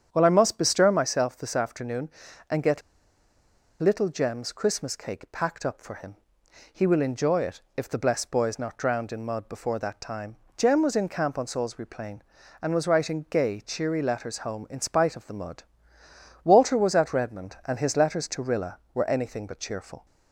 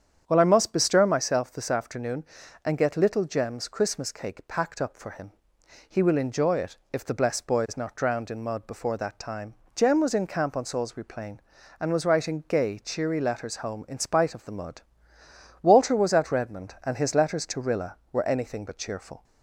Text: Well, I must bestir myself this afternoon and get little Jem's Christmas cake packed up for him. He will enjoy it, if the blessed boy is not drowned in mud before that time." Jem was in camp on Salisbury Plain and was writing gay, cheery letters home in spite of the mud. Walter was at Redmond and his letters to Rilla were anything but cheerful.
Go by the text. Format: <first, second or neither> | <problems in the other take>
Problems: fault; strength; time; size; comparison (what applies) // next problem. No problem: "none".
second | starts louder than the rest; strong; until 1.1 s; 8.5 dB; strong in the second // pauses between "get" and "little"; at 2.8 s; 1.0 s long